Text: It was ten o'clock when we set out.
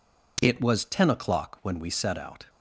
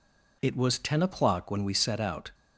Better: neither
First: none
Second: none

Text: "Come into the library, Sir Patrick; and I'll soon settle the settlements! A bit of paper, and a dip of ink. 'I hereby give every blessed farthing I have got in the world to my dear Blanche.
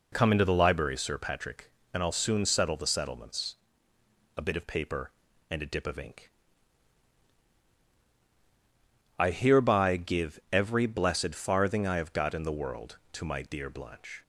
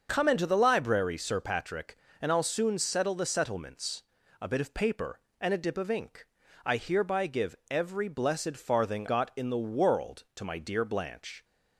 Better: first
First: none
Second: starts louder than the rest; until 1.1 s; 6.5 dB // pauses between "give" and "every"; slight; at 7.5 s; 0.16 s long // skips "I have"; at 9.0 s

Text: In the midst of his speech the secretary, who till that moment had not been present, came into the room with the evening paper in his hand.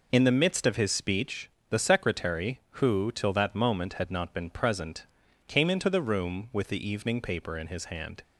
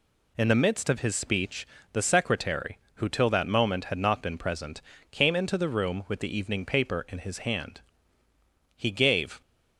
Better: first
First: pauses between "speech" and "the"; slight; at 1.5 s; 0.20 s long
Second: pauses between "speech" and "the"; slight; at 1.6 s; 0.26 s long // goes on to say "He gave"; noticeable; from 8.7 s on; 0.66 s long

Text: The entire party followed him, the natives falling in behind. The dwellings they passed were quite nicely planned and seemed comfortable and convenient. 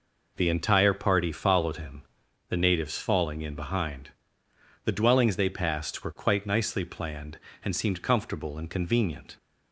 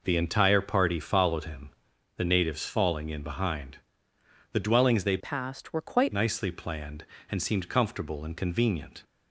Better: first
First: none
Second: changes voice from "passed" to "quite"; from 5.1 to 6.1 s; 1.0 s long

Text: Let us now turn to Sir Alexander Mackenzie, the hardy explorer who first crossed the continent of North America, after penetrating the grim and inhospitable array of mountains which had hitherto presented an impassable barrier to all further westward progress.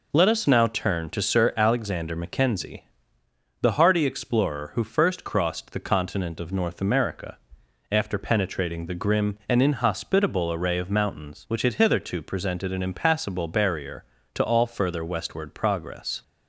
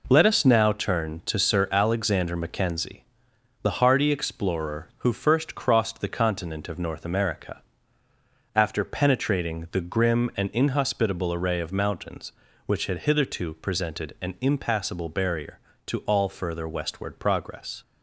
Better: neither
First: none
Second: none

